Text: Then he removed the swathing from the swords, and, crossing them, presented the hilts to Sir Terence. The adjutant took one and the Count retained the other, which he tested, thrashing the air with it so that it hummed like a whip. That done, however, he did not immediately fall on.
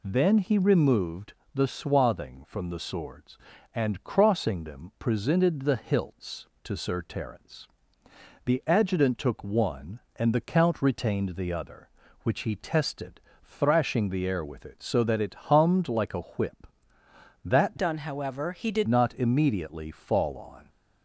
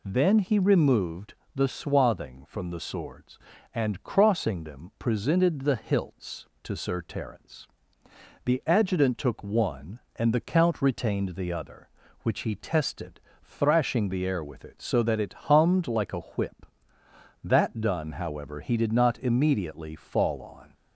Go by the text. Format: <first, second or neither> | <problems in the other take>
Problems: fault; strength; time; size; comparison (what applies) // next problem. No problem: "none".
second | pauses between "removed" and "the"; slight; at 1.3 s; 0.20 s long; slight in the second // changes voice from "done" to "did"; from 17.7 to 18.8 s; 1.1 s long